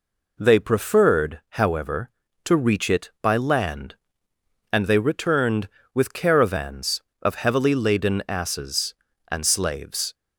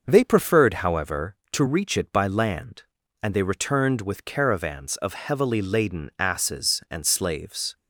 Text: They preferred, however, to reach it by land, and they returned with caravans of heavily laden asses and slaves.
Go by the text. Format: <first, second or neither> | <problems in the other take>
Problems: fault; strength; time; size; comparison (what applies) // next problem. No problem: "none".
first | starts louder than the rest; noticeable; until 1.1 s; 6 dB